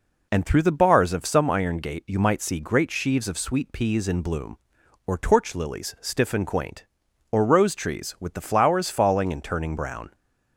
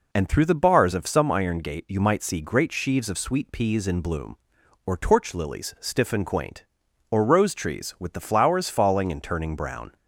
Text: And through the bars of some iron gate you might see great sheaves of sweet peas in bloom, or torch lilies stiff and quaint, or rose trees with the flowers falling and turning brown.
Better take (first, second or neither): neither